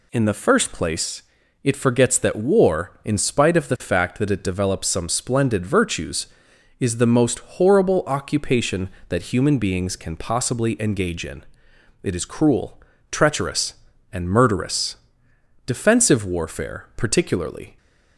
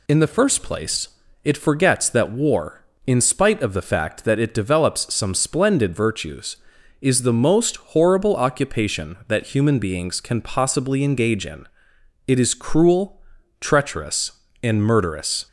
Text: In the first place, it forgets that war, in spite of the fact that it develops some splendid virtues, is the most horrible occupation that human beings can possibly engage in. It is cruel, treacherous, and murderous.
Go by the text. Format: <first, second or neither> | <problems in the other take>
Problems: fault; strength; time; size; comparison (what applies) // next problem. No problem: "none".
second | goes on to say "Defensive warfare particularly"; strong; from 15.6 s on; 2.1 s long